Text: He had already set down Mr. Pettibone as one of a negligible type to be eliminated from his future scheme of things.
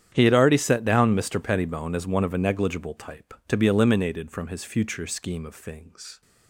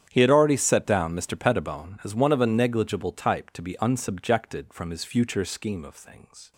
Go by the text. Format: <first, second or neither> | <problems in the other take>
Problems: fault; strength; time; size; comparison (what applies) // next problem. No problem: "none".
first | starts louder than the rest; strong; until 1.1 s; 9 dB; strong in the first // says "unsubjected" for "eliminated"; at 3.7 s